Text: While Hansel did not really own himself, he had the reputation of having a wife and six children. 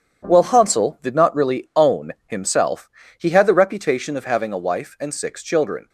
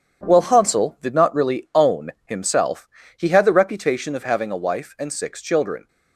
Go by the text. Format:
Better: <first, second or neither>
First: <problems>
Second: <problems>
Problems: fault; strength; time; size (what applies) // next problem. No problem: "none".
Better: neither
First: starts louder than the rest; strong; until 1.3 s; 8.5 dB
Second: starts louder than the rest; strong; until 1.3 s; 8.5 dB